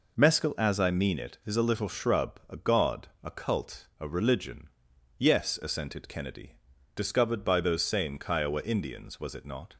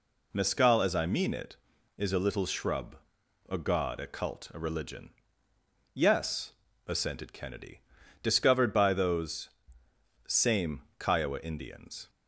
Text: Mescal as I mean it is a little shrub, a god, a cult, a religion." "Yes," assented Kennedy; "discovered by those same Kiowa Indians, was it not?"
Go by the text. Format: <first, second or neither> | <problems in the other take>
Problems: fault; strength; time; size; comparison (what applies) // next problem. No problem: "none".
first | pauses between "those" and "same"; noticeable; at 9.4 s; 0.78 s long // pauses between "same" and "Kiowa"; slight; at 10.8 s; 0.16 s long // stops before "was it not"; at 12.0 s